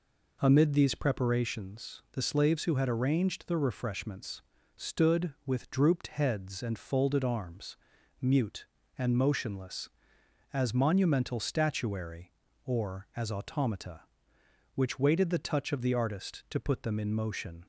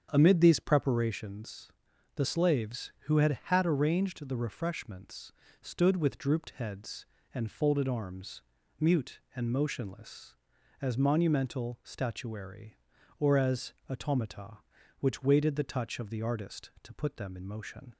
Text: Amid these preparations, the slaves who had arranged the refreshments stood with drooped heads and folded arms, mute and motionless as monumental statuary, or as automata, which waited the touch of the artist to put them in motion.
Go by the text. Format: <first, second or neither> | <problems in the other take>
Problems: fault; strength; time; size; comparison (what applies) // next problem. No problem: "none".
first | starts louder than the rest; strong; until 1.1 s; 7.5 dB // says "had" twice; at 3.4 s // pauses between "refreshments" and "stood"; slight; at 5.3 s; 0.28 s long; also in the first // pauses between "as" and "automata"; slight; at 13.7 s; 0.16 s long